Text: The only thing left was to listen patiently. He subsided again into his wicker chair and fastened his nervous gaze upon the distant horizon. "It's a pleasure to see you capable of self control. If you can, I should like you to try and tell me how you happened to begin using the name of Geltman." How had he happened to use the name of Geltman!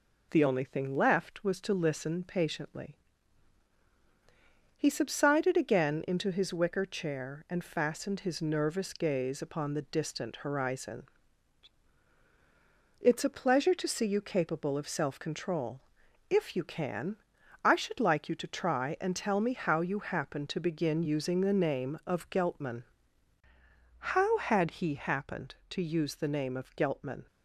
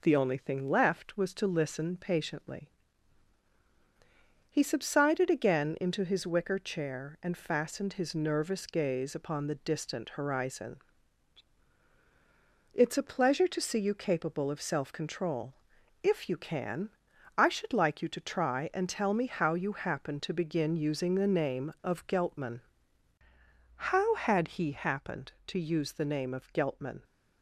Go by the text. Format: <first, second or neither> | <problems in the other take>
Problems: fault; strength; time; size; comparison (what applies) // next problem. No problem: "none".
neither | none